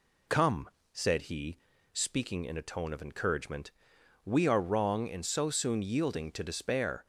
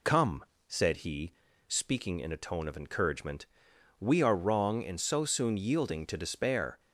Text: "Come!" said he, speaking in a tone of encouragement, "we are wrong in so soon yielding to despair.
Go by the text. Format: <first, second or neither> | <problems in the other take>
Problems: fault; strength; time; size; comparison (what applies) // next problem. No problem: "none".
neither | none